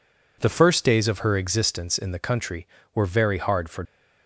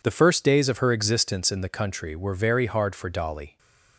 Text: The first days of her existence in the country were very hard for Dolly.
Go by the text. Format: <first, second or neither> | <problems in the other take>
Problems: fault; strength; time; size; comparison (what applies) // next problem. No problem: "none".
second | stops before "Dolly"; at 3.8 s